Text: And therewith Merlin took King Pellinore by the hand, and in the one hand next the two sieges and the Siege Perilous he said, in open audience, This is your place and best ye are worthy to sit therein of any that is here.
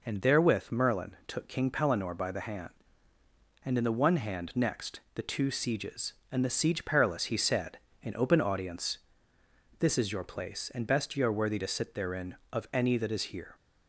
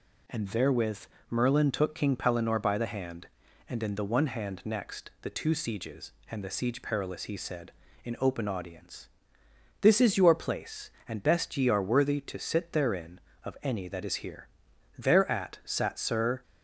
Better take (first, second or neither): first